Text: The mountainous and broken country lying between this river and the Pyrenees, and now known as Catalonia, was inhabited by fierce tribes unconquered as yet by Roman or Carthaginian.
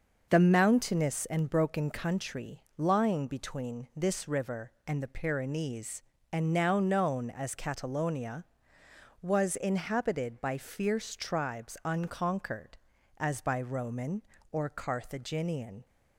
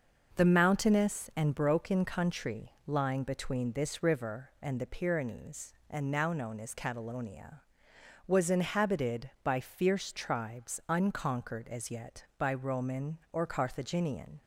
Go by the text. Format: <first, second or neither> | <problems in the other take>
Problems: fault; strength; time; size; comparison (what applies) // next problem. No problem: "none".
second | starts louder than the rest; until 1.2 s; 6.5 dB; noticeable in the second // pauses between "country" and "lying"; slight; at 2.6 s; 0.16 s long // skips "yet"; at 13.4 s